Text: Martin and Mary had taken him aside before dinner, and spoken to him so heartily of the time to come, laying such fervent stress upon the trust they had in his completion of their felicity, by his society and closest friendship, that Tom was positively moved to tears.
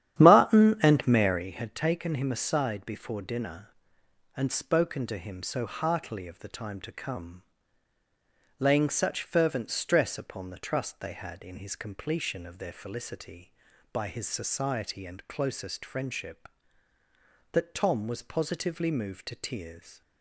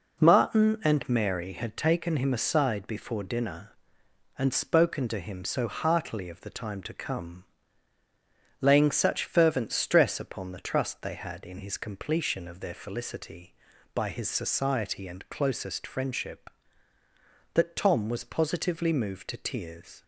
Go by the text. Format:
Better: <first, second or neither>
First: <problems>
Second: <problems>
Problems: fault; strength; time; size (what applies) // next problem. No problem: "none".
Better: second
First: starts louder than the rest; strong; until 1.5 s; 10.5 dB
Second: none